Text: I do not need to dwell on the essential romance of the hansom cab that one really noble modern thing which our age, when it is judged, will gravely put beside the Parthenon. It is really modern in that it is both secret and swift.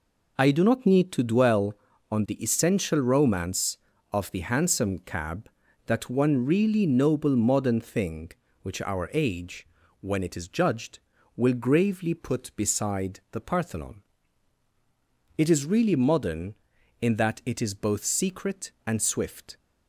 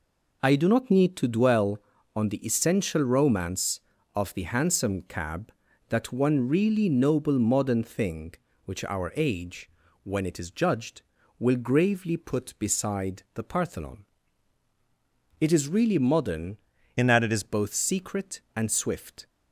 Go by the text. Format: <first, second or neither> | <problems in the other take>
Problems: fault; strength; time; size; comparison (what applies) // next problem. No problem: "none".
first | changes voice from "in" to "is"; from 16.9 to 17.4 s; 0.5 s long